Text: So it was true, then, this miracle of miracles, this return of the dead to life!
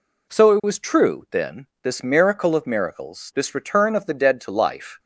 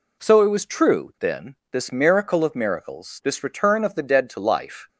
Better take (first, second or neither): neither